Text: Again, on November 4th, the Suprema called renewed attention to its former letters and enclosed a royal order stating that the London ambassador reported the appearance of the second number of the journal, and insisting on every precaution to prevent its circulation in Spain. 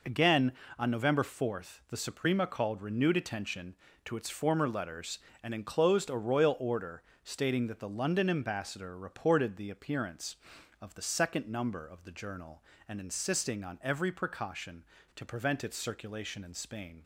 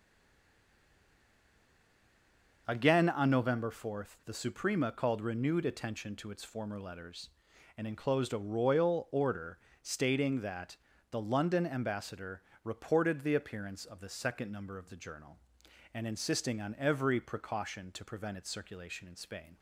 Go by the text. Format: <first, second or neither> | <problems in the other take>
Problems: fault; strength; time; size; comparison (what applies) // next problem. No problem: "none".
first | stays silent before the first word; strong; until 2.6 s; 2.6 s long // pauses between "order" and "stating"; slight; at 9.5 s; 0.26 s long; slight in the first // pauses between "that" and "the"; slight; at 10.7 s; 0.34 s long // pauses between "ambassador" and "reported"; slight; at 12.4 s; 0.22 s long